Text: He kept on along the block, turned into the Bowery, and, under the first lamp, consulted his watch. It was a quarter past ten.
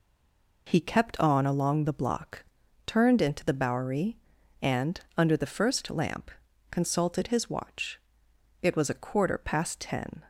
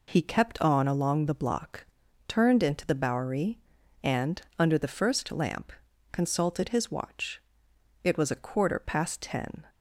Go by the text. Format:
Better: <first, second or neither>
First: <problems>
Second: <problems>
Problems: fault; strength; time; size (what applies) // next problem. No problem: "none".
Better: second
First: stays silent before the first word; slight; until 0.6 s; 0.6 s long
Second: none